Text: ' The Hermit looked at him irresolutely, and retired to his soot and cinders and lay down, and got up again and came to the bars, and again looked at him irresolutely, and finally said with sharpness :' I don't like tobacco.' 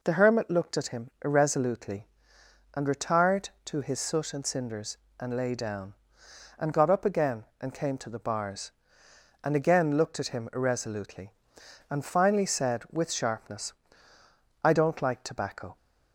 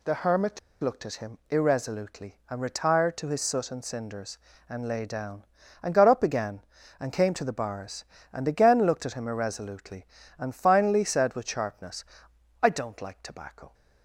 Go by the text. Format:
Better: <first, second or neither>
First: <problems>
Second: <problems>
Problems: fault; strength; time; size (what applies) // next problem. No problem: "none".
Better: first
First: none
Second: pauses between "Hermit" and "looked"; slight; at 0.5 s; 0.21 s long